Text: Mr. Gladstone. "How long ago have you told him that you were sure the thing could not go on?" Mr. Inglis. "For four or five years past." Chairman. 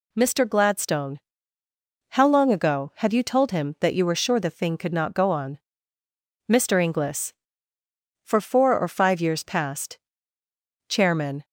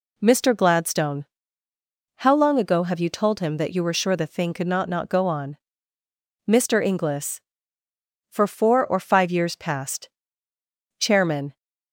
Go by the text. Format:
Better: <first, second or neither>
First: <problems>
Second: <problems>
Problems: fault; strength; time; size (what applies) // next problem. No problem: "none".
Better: first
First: none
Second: says "not" twice; at 4.8 s